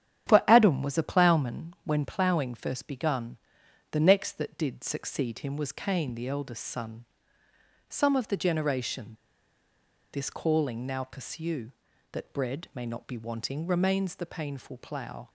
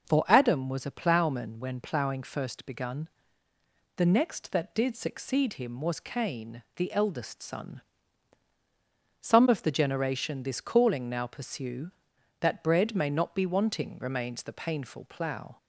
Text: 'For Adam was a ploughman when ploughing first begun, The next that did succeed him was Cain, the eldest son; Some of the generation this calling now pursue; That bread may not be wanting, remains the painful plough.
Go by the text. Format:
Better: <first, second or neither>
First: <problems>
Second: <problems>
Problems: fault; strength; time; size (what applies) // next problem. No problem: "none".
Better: second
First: starts louder than the rest; strong; until 1.3 s; 9.5 dB // pauses between "generation" and "this"; noticeable; at 9.1 s; 0.98 s long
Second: starts louder than the rest; noticeable; until 1.1 s; 6 dB